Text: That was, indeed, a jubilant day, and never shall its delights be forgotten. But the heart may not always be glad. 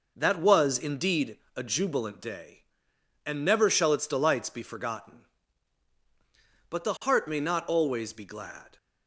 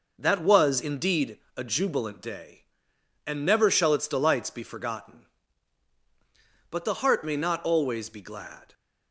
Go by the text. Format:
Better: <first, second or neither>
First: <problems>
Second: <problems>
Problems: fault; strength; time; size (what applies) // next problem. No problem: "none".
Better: neither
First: none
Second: none